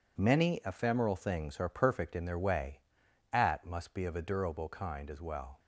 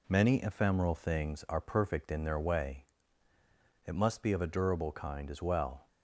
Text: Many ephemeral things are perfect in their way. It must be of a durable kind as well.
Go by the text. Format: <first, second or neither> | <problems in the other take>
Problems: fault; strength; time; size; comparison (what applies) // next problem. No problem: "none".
second | says "At" for "It"; at 3.3 s